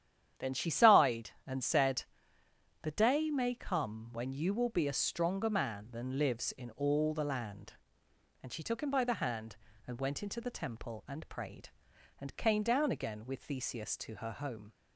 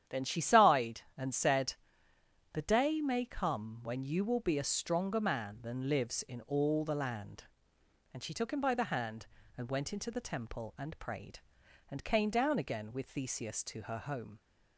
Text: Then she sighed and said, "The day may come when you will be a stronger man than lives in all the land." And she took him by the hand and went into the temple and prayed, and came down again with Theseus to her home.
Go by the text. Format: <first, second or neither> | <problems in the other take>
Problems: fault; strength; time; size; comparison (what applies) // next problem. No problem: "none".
neither | starts louder than the rest; strong; the same in both